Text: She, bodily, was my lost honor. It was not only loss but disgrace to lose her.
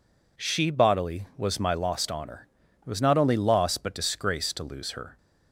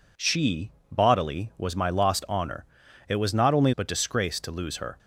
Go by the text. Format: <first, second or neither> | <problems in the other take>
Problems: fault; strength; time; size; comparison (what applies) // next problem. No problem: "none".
first | skips "loss"; at 3.7 s